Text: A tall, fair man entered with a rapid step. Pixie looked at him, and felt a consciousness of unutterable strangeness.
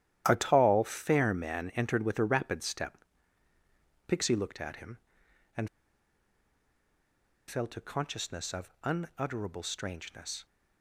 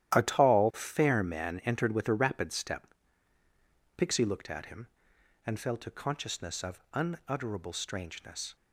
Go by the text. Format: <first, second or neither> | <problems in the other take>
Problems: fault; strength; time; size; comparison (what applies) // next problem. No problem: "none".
second | starts louder than the rest; strong; until 1.2 s; 12.5 dB; strong in the second // pauses between "and" and "felt"; strong; at 5.6 s; 1.8 s long